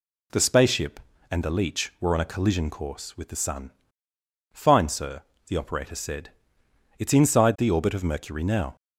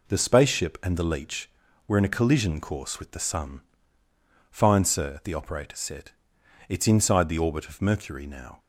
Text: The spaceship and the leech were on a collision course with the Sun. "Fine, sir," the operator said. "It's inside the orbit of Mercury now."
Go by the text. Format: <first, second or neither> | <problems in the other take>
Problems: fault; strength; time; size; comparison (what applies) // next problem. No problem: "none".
first | says "in" for "on"; at 1.9 s